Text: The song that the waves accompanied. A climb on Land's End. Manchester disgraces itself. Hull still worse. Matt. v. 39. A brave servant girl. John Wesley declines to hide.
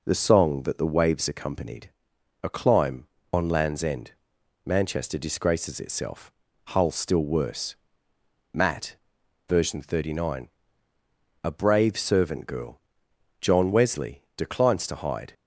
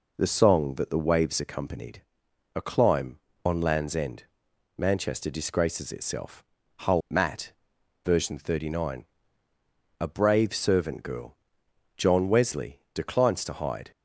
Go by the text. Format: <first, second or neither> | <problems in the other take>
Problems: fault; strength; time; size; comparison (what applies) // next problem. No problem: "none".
first | skips "still worse"; at 7.0 s